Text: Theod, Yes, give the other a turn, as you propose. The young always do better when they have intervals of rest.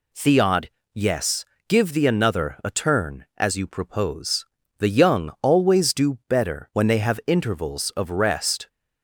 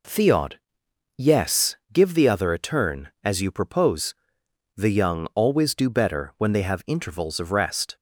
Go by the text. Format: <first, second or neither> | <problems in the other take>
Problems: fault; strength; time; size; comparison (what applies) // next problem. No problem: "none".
second | says "another" for "other"; at 2.0 s